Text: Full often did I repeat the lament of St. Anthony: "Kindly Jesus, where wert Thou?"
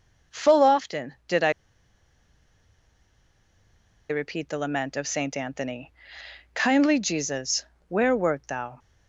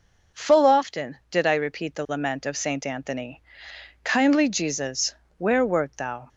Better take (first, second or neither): second